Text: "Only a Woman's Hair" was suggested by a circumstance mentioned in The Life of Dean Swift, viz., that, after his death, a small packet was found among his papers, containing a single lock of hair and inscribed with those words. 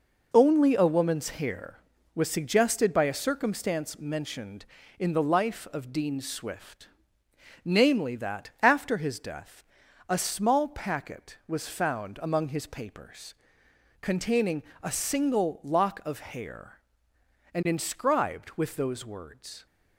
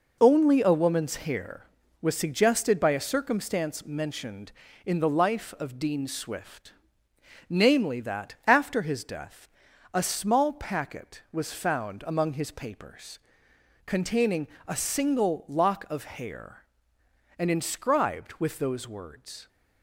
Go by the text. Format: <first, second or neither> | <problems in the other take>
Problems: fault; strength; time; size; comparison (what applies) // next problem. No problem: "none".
neither | pauses between "containing" and "a"; slight; the same in both